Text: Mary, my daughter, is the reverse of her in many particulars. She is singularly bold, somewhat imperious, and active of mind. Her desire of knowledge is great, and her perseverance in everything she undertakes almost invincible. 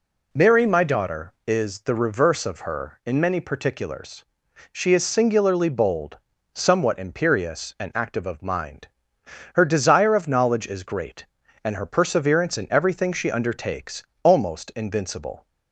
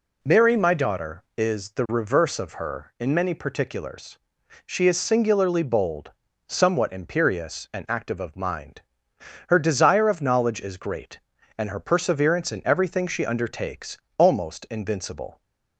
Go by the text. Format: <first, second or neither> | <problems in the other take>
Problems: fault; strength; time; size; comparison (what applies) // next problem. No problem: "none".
neither | pauses between "undertakes" and "almost"; slight; the same in both